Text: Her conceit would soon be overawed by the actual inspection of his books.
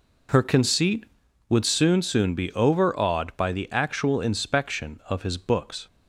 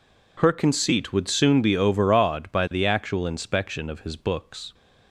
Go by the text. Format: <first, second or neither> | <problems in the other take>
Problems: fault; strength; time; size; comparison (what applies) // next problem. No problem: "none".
second | says "soon" twice; at 2.0 s